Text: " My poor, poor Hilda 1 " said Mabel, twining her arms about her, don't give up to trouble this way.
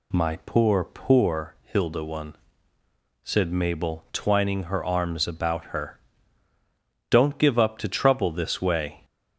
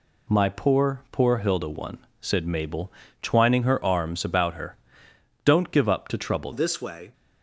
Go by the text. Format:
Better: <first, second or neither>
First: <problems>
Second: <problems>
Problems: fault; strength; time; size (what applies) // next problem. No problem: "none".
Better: first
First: none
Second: changes voice at "this"; from 6.5 s on; 0.6 s long